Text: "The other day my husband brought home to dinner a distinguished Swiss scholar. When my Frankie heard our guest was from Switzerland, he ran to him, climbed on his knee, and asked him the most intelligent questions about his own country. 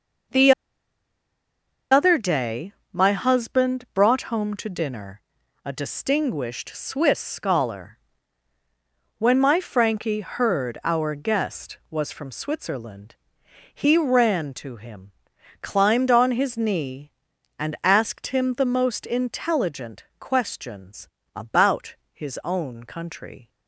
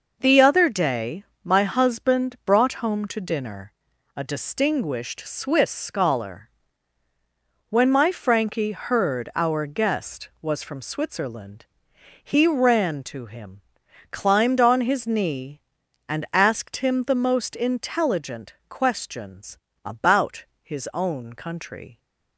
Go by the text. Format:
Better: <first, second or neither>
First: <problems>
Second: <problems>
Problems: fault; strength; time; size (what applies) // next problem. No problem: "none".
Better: second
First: pauses between "The" and "other"; strong; at 0.5 s; 1.3 s long // pauses between "day" and "my"; slight; at 2.7 s; 0.20 s long // pauses between "dinner" and "a"; at 5.1 s; 0.44 s long // pauses between "intelligent" and "questions"; slight; at 20.0 s; 0.16 s long // pauses between "questions" and "about"; slight; at 21.0 s; 0.26 s long // pauses between "about" and "his"; slight; at 21.9 s; 0.16 s long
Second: pauses between "day" and "my"; slight; at 1.2 s; 0.20 s long // pauses between "dinner" and "a"; at 3.7 s; 0.44 s long // pauses between "intelligent" and "questions"; slight; at 18.5 s; 0.16 s long // pauses between "questions" and "about"; slight; at 19.5 s; 0.26 s long // pauses between "about" and "his"; slight; at 20.4 s; 0.16 s long